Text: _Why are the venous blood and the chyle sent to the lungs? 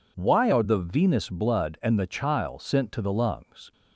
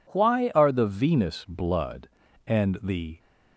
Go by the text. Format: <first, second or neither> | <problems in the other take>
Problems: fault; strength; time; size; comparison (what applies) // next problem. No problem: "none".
first | stops before "chyle sent to the lungs"; at 3.1 s